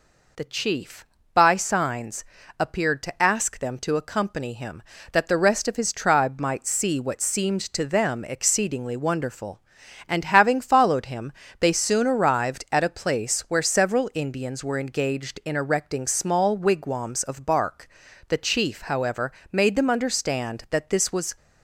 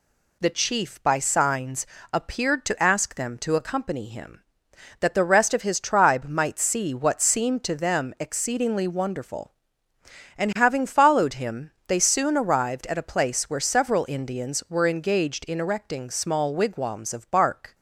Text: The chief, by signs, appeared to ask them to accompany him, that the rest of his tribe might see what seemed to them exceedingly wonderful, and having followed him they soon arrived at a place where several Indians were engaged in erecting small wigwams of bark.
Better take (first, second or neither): second